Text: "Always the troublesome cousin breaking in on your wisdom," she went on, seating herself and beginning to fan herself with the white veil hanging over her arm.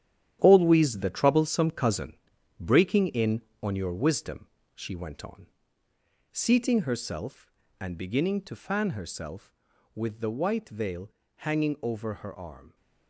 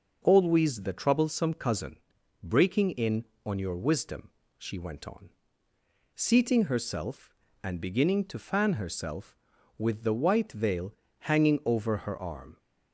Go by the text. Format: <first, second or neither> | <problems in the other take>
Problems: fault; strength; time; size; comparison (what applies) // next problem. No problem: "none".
second | gets quieter; strong; throughout; 10 dB // pauses between "cousin" and "breaking"; noticeable; at 2.1 s; 0.46 s long; noticeable in the second // pauses between "veil" and "hanging"; slight; at 11.1 s; 0.28 s long; slight in the second